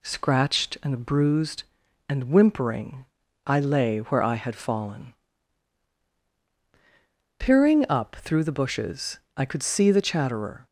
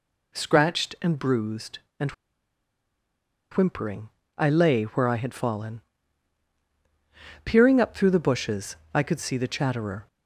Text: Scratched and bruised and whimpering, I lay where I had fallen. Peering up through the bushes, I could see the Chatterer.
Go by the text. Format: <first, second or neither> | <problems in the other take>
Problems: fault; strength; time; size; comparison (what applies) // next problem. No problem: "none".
first | pauses between "and" and "whimpering"; strong; at 2.1 s; 1.4 s long